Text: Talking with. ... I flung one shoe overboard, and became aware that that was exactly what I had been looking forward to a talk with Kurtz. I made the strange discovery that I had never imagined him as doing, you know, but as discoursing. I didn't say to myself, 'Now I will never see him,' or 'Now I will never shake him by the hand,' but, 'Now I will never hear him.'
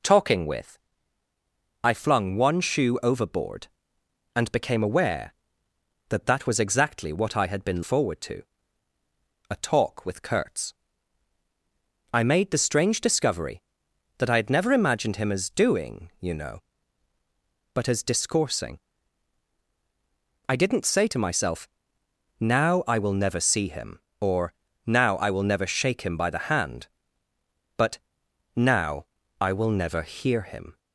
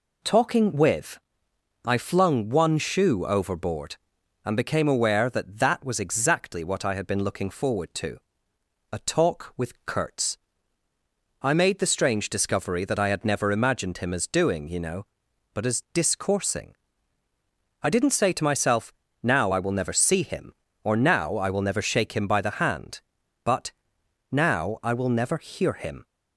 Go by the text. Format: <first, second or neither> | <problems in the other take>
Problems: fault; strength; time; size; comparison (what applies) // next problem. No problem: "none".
second | skips "looking"; at 7.8 s // pauses between "to" and "a"; at 8.4 s; 1.0 s long; noticeable in the second // pauses between "or" and "Now"; slight; at 24.5 s; 0.32 s long // pauses between "Now" and "I"; at 29.0 s; 0.38 s long